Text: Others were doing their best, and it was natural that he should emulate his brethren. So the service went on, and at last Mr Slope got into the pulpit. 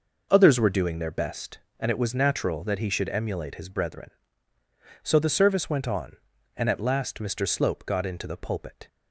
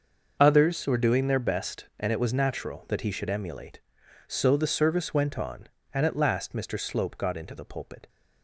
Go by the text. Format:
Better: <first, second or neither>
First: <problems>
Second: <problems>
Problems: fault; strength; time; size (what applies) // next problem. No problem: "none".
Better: first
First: none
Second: starts louder than the rest; until 1.4 s; 6.5 dB // skips "his brethren"; at 4.0 s